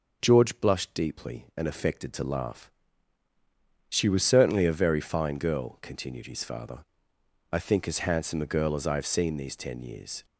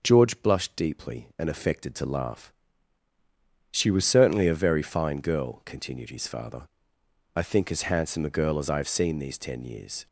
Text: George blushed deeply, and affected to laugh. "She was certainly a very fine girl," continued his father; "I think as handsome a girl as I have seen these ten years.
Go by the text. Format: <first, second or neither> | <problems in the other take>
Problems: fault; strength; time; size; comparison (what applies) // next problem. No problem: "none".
neither | none